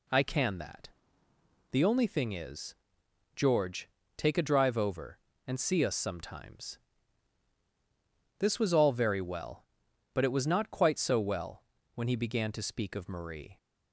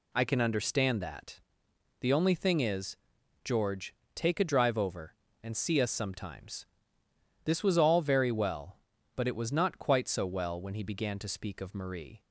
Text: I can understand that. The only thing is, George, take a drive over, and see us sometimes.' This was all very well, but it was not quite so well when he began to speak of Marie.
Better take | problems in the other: second | skips "understand"; at 0.5 s // pauses between "well" and "when"; slight; at 11.6 s; 0.32 s long

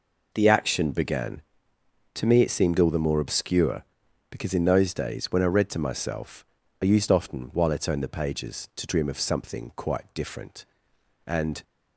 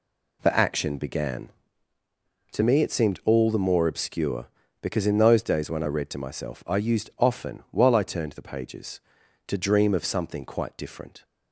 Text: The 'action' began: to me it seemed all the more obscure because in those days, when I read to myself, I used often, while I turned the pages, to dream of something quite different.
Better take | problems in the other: second | goes on to say "And"; slight; from 11.2 s on; 0.38 s long

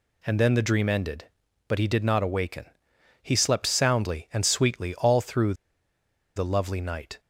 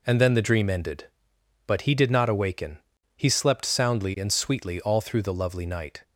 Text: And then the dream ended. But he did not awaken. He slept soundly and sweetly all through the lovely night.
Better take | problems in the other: second | pauses between "through" and "the"; noticeable; at 5.5 s; 0.82 s long

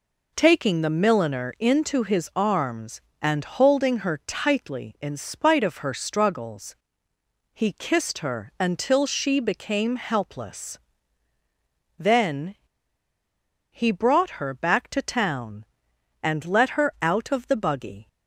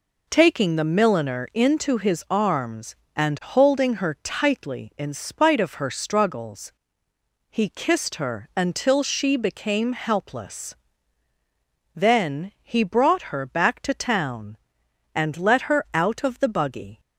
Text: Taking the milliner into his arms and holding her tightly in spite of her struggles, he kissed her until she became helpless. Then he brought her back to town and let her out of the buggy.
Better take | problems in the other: second | pauses between "Then" and "he"; at 12.5 s; 1.1 s long

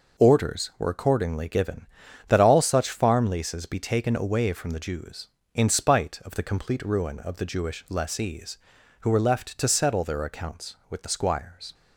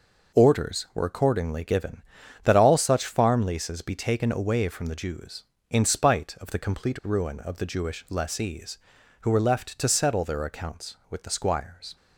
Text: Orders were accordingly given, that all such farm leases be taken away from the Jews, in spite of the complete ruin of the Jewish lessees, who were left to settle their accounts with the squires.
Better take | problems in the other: neither | none

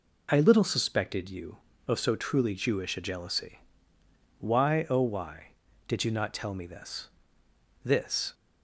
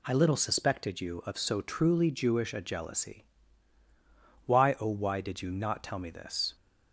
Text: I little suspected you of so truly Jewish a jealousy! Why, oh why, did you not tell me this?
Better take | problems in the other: second | says "this" twice; at 7.8 s

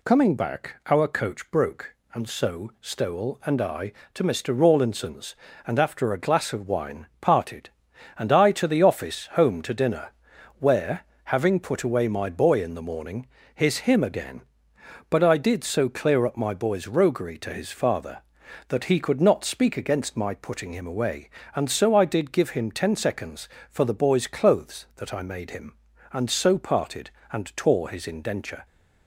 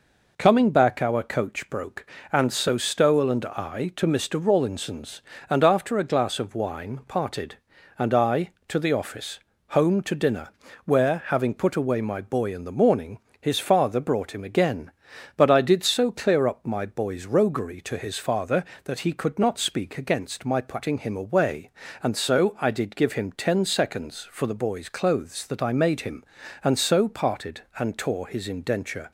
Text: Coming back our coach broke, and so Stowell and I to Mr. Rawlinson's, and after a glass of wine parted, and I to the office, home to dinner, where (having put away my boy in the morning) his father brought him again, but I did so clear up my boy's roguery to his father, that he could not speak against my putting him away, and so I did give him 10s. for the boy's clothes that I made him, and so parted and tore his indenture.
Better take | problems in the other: second | pauses between "wine" and "parted"; slight; at 7.0 s; 0.16 s long // skips "father brought"; at 13.8 s

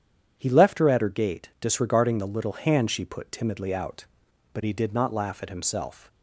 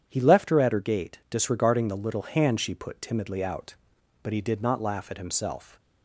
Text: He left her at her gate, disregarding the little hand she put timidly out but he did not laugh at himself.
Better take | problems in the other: neither | starts louder than the rest; strong; the same in both

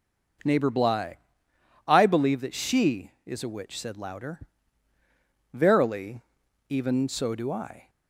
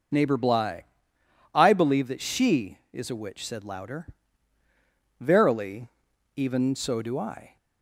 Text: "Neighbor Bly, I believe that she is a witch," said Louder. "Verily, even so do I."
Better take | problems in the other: first | loses the start of "Neighbor"; at 0.1 s; 40 ms

